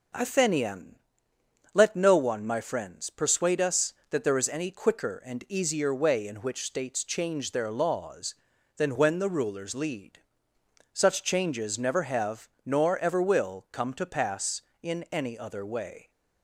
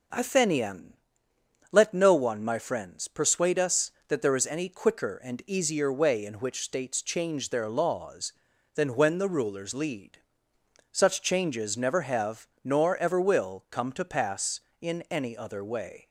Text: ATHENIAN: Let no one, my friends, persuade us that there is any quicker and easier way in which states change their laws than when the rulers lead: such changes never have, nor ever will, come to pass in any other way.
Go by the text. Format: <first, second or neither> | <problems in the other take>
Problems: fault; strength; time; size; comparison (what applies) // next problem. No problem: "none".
neither | none